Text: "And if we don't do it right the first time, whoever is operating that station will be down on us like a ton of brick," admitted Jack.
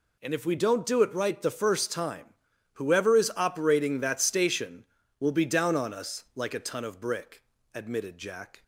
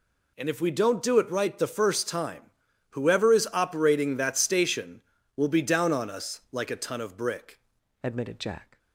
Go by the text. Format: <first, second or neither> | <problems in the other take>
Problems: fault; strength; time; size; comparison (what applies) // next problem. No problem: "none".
first | changes voice at "admitted"; from 8.0 s on; 0.7 s long